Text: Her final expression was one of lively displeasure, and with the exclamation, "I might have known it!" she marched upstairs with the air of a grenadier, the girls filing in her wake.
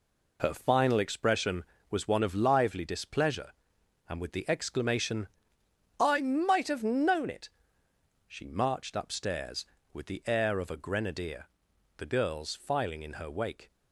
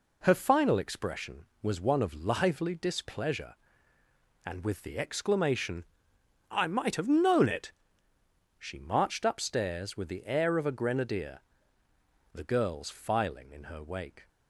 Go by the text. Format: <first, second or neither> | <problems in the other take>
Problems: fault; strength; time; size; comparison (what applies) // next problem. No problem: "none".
neither | none